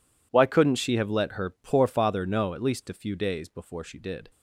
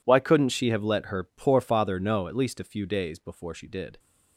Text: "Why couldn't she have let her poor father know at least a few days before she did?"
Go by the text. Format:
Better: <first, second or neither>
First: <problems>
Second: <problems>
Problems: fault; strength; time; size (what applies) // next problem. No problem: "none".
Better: neither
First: none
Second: none